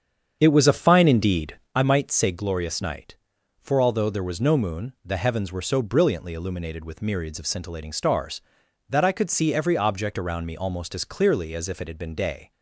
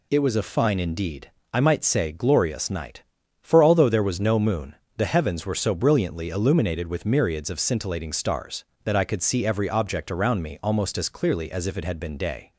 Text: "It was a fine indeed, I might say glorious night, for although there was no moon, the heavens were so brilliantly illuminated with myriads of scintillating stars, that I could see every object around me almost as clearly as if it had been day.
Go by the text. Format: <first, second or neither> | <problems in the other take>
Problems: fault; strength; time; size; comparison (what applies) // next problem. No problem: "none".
second | starts louder than the rest; strong; until 1.8 s; 7.5 dB